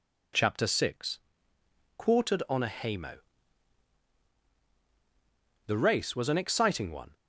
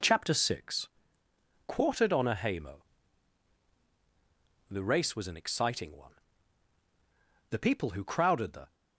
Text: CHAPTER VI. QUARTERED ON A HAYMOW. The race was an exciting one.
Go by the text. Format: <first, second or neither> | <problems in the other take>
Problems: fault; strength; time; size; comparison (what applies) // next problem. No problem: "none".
first | goes on to say "The people who crowded the"; noticeable; from 7.5 s on; 1.2 s long